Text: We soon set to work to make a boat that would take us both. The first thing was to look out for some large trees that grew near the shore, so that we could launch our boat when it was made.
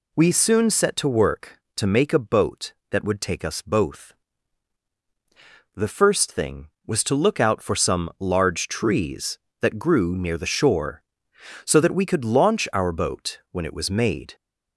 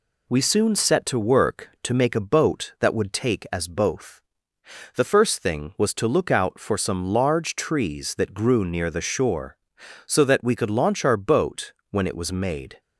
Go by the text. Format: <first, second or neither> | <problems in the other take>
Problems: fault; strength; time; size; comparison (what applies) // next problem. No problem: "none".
first | says "as" for "us"; at 3.5 s // pauses between "boat" and "when"; slight; at 11.7 s; 0.18 s long